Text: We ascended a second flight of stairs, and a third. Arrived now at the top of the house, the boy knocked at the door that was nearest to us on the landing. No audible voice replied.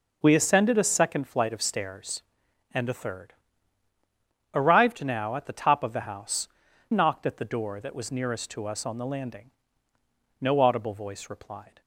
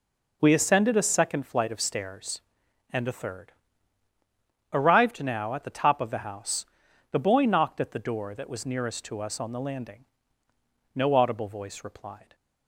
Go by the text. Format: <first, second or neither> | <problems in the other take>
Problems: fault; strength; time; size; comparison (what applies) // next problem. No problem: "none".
second | skips "the boy"; at 6.6 s